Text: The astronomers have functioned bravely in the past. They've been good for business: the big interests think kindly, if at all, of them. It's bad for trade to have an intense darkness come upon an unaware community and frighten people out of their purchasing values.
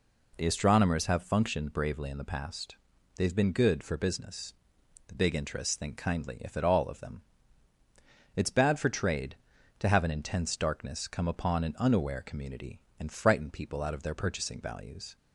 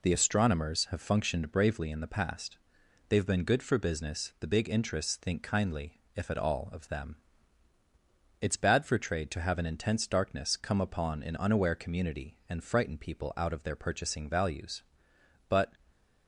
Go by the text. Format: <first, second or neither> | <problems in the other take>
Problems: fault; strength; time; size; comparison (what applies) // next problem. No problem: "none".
first | goes on to say "But"; slight; from 15.4 s on; 0.28 s long